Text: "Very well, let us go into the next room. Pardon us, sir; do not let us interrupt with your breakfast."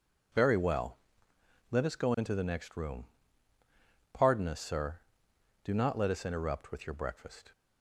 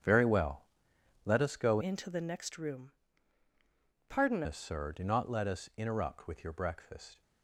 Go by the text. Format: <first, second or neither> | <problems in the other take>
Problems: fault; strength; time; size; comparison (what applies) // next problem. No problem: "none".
first | starts louder than the rest; strong; until 1.6 s; 7.5 dB // changes voice from "into" to "Pardon"; from 1.8 to 4.4 s; 2.6 s long